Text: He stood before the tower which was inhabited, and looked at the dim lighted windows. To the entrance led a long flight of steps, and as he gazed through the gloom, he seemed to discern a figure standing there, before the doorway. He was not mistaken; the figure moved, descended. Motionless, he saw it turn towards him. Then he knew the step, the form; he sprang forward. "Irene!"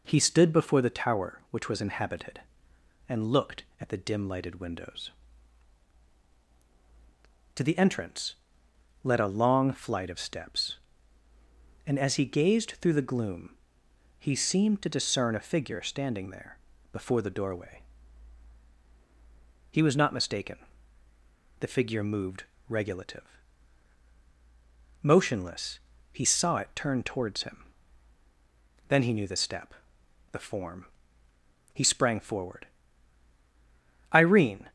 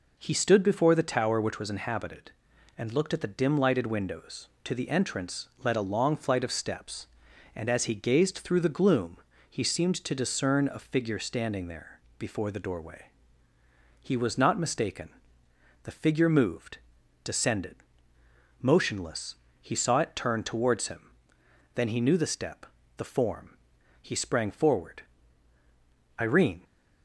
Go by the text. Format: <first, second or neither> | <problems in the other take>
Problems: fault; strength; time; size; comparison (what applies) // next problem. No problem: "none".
second | pauses between "entrance" and "led"; noticeable; at 8.3 s; 0.66 s long; slight in the second // says "regulative" for "descended"; at 22.6 s